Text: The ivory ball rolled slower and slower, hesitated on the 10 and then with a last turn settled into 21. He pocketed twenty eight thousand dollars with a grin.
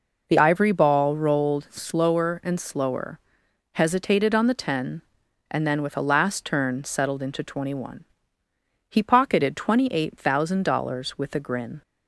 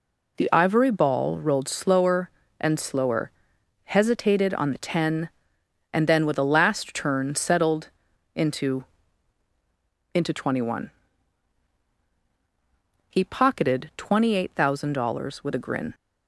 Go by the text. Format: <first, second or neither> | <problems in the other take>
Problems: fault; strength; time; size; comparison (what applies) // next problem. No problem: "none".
first | pauses between "settled" and "into"; noticeable; at 7.8 s; 0.46 s long // says "into" twice; at 10.1 s